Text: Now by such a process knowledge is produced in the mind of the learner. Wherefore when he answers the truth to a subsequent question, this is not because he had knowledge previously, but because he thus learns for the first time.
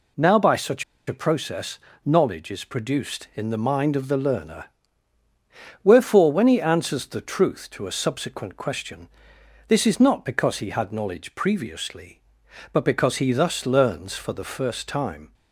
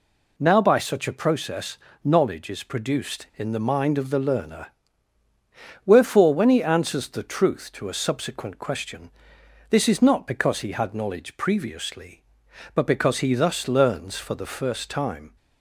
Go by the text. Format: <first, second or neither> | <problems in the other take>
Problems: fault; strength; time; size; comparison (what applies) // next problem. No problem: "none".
second | pauses between "such" and "a"; slight; at 0.8 s; 0.23 s long // pauses between "process" and "knowledge"; slight; at 1.7 s; 0.26 s long; slight in the second